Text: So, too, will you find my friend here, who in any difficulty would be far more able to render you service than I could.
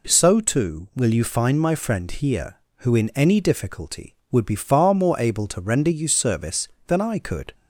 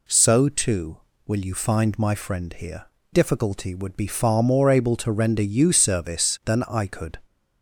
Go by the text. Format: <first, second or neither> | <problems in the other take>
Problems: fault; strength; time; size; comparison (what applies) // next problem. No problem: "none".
first | skips "who in any"; at 2.9 s